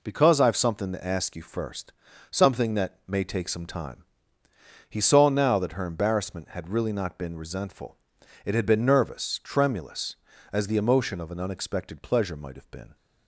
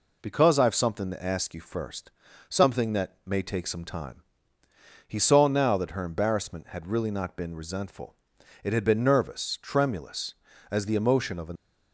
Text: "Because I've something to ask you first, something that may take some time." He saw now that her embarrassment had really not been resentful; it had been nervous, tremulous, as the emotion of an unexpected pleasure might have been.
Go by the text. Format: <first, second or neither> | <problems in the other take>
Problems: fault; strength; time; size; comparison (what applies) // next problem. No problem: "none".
first | stops before "unexpected pleasure might have been"; at 11.5 s